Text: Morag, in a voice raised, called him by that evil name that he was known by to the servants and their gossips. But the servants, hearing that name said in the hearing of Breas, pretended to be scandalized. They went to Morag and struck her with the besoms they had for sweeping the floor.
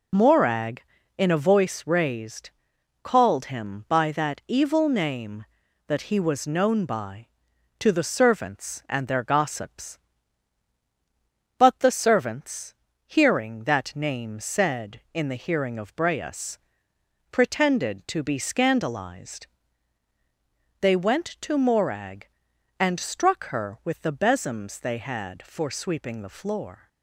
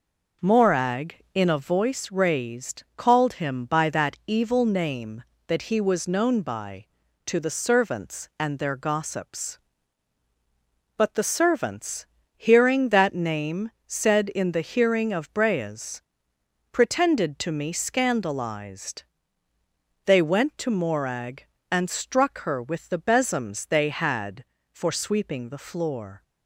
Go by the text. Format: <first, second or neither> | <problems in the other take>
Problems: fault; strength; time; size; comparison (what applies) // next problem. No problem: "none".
first | pauses between "name" and "said"; slight; at 13.7 s; 0.16 s long // says "me" for "be"; at 17.5 s